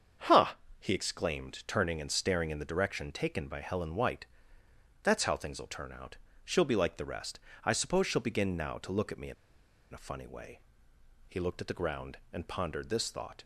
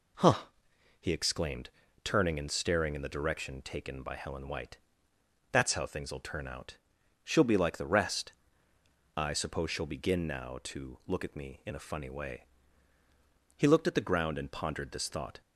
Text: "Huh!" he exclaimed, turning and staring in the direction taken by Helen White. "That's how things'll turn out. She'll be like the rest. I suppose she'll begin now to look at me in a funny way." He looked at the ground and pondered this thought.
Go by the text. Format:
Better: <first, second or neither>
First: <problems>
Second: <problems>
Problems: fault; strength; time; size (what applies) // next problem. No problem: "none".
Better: second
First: starts louder than the rest; until 1.4 s; 7 dB // pauses between "in" and "a"; noticeable; at 9.3 s; 0.59 s long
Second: none